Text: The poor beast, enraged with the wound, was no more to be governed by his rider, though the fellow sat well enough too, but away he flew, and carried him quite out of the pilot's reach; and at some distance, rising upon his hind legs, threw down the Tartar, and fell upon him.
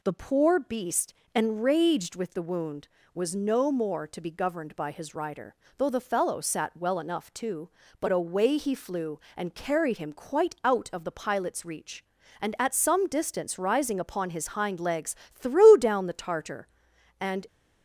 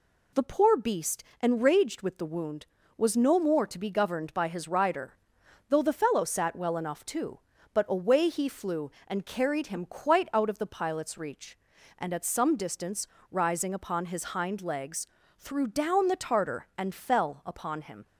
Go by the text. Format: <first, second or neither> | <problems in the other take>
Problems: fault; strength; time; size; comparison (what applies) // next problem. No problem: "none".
second | stops before "fell upon him"; at 17.4 s